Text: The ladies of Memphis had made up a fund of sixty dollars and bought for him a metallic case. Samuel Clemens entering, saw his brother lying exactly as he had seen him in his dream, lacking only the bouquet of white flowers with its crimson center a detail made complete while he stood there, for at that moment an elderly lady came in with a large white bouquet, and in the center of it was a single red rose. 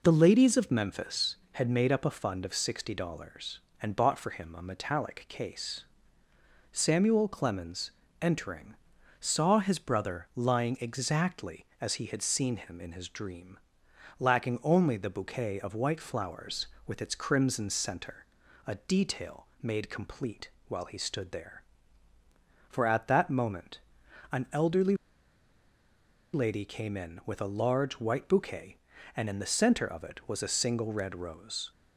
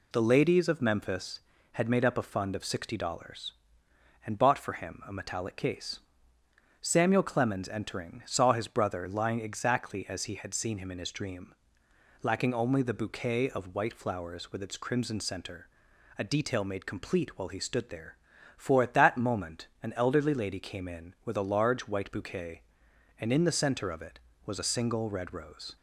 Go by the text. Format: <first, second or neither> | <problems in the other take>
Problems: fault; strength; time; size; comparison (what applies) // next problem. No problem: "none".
second | pauses between "Clemens" and "entering"; slight; at 7.9 s; 0.28 s long // pauses between "center" and "a"; at 18.2 s; 0.40 s long; noticeable in the second // pauses between "detail" and "made"; slight; at 19.4 s; 0.16 s long // pauses between "complete" and "while"; slight; at 20.4 s; 0.16 s long // pauses between "moment" and "an"; noticeable; at 23.7 s; 0.54 s long // pauses between "elderly" and "lady"; strong; at 24.9 s; 1.3 s long